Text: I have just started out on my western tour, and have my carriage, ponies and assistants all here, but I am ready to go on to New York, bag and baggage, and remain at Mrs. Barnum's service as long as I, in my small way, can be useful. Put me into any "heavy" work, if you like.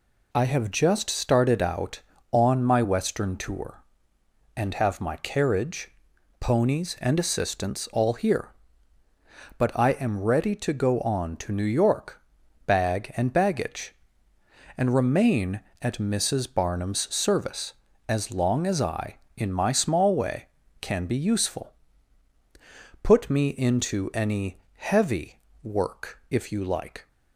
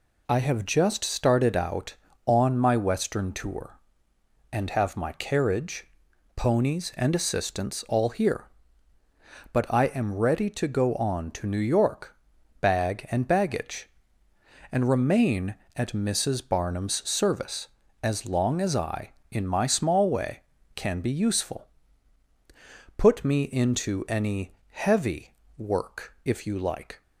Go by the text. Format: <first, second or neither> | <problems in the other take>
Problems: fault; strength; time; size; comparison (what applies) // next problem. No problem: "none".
neither | pauses between "any" and "heavy"; slight; the same in both // pauses between "heavy" and "work"; slight; the same in both